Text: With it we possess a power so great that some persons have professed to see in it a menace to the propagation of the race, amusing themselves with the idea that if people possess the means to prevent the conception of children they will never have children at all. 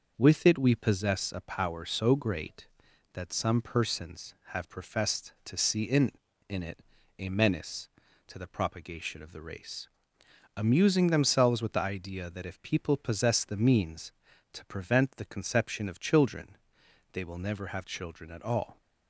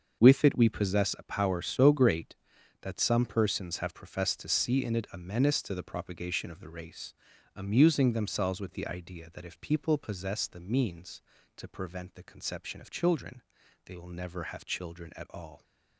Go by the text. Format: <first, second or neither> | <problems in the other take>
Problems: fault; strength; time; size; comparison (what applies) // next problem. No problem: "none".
second | starts louder than the rest; noticeable; until 1.1 s; 6 dB; also in the second // says "in" twice; at 6.4 s // pauses between "it" and "a"; at 6.8 s; 0.38 s long // pauses between "children" and "they"; noticeable; at 16.5 s; 0.56 s long; also in the second